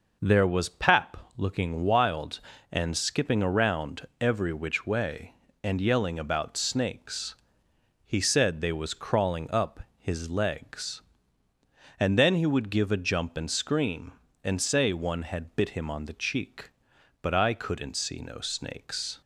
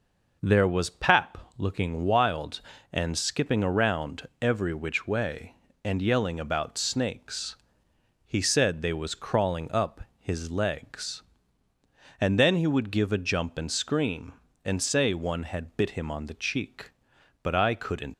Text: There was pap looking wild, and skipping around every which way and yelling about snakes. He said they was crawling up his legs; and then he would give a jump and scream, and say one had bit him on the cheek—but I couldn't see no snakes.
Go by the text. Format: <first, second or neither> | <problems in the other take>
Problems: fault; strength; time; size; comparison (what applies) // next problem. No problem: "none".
first | pauses between "pap" and "looking"; slight; at 1.3 s; 0.20 s long; slight in the first // stops before "see no snakes"; at 18.1 s